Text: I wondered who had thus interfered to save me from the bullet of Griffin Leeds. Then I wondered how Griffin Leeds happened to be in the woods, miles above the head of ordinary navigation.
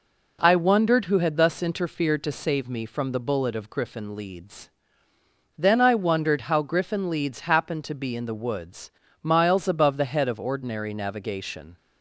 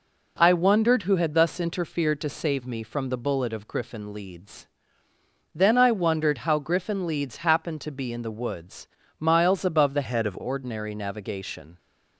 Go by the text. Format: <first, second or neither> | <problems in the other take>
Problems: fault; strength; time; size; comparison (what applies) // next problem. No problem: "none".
first | changes voice from "head" to "of"; from 10.0 to 10.3 s; 0.3 s long